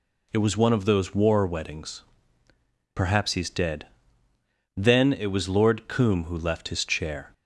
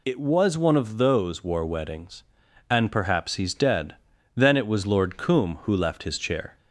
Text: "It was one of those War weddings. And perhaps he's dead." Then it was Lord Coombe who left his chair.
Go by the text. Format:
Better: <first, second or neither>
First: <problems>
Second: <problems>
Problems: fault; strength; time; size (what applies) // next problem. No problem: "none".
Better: second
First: skips "And"; at 2.4 s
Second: none